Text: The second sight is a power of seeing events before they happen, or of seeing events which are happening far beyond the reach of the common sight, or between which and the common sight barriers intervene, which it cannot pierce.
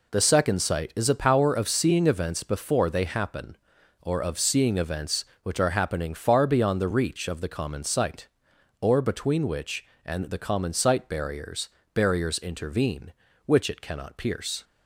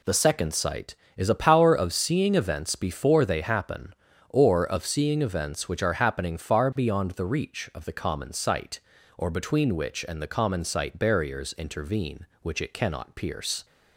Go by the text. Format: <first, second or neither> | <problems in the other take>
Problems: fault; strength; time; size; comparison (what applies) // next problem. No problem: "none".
second | says "barriers" twice; at 11.9 s